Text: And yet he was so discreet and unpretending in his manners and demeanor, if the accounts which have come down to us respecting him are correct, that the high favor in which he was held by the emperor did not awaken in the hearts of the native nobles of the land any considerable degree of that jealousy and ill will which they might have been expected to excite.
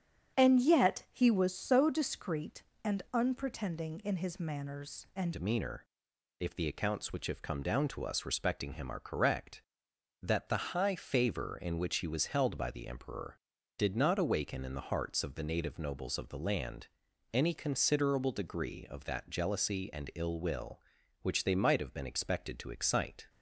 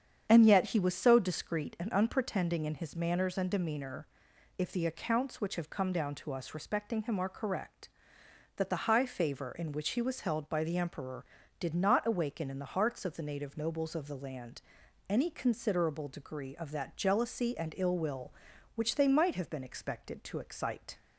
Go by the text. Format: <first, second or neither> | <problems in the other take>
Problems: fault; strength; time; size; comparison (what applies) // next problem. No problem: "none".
second | starts louder than the rest; strong; until 1.4 s; 8 dB; strong in the second // changes voice at "demeanor"; from 5.3 s on; 17.9 s long // pauses between "land" and "any"; at 16.8 s; 0.44 s long; noticeable in the second